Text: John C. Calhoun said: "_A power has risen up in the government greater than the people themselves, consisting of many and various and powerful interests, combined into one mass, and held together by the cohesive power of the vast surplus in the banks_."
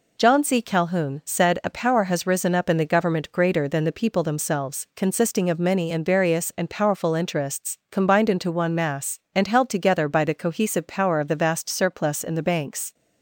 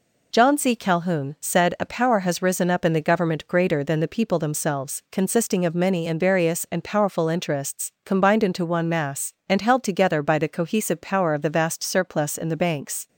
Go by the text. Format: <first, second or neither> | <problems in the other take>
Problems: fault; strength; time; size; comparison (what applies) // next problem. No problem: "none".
neither | none